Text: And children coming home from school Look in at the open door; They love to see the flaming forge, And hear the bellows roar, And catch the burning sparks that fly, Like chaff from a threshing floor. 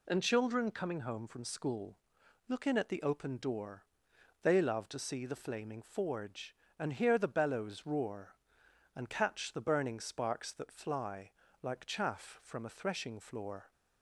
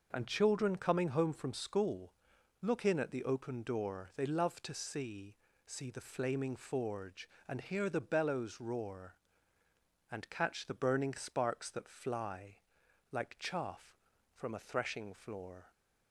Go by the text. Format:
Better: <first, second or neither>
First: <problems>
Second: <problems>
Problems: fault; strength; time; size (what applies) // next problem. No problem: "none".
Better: first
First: pauses between "school" and "Look"; noticeable; at 1.9 s; 0.52 s long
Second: pauses between "school" and "Look"; noticeable; at 2.1 s; 0.50 s long // says "see" twice; at 5.6 s